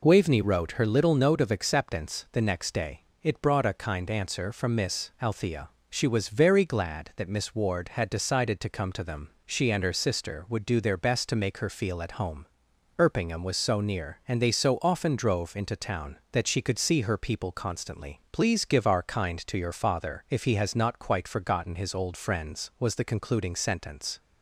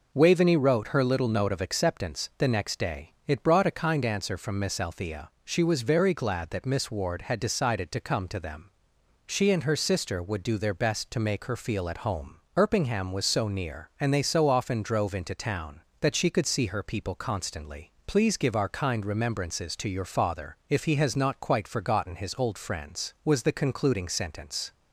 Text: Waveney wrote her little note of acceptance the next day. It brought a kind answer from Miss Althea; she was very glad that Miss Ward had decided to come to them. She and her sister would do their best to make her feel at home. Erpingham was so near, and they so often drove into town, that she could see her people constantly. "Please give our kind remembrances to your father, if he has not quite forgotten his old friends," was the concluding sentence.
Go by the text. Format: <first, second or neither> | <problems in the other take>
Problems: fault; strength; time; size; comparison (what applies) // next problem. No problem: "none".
second | skips "remembrances"; at 19.4 s